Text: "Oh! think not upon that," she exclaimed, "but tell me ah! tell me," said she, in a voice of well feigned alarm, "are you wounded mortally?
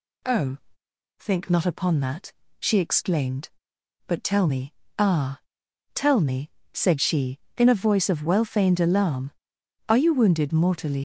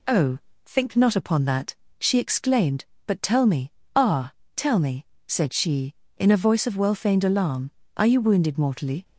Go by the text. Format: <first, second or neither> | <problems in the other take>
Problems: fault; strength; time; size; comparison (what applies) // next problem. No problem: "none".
second | pauses between "me" and "ah"; slight; at 4.7 s; 0.26 s long; slight in the second // leaves "mortally" unfinished; at 10.9 s; 120 ms